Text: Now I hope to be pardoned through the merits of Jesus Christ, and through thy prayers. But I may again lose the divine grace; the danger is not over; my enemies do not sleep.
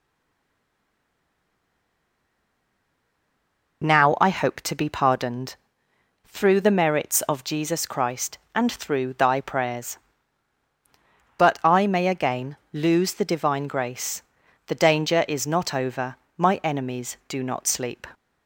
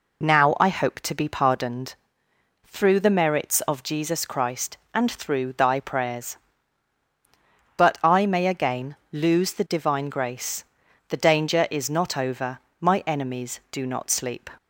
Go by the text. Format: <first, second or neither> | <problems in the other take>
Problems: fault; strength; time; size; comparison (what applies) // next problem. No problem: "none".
second | stays silent before the first word; strong; until 3.8 s; 3.8 s long // pauses between "pardoned" and "through"; noticeable; at 5.5 s; 0.68 s long; noticeable in the second // pauses between "again" and "lose"; slight; at 12.5 s; 0.16 s long; slight in the second